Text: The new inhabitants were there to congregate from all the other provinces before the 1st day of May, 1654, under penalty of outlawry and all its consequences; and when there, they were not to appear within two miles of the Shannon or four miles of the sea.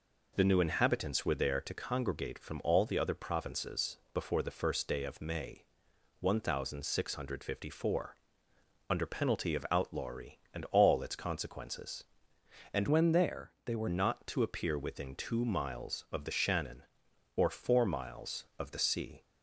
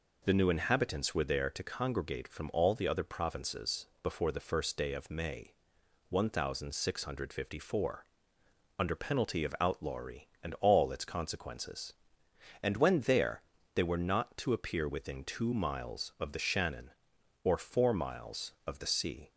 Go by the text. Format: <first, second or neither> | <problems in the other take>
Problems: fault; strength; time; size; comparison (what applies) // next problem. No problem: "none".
second | changes voice from "when" to "were"; from 12.8 to 13.8 s; 1.0 s long